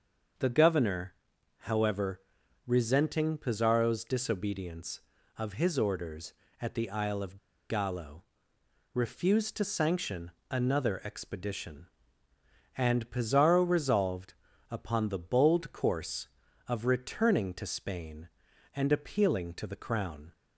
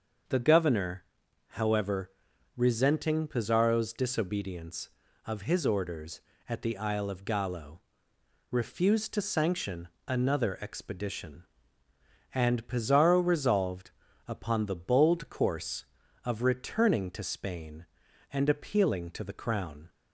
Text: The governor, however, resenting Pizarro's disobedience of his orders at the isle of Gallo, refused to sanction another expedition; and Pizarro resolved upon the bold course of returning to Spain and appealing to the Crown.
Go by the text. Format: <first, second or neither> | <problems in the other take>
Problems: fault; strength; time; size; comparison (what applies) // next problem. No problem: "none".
second | starts louder than the rest; until 1.8 s; 6.5 dB; also in the second // pauses between "of" and "Gallo"; slight; at 7.3 s; 0.31 s long // pauses between "sanction" and "another"; slight; at 10.3 s; 0.18 s long; slight in the second // pauses between "resolved" and "upon"; slight; at 14.3 s; 0.34 s long; slight in the second